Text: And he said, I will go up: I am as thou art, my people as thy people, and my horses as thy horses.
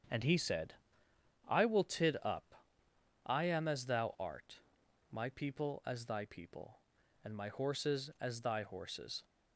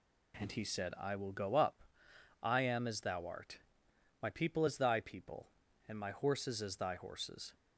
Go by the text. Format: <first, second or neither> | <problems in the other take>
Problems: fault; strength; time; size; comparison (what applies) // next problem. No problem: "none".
second | starts louder than the rest; strong; until 1.8 s; 7.5 dB // says "tid" for "go"; at 1.8 s